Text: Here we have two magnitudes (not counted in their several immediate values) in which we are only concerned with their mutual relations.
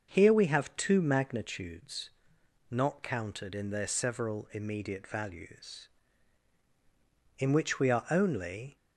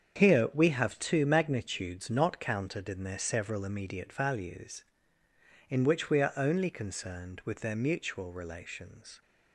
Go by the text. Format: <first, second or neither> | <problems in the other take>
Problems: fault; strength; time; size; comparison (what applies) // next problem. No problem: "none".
second | starts louder than the rest; until 1.1 s; 6.5 dB; strong in the second // stops before "concerned with their mutual relations"; at 8.7 s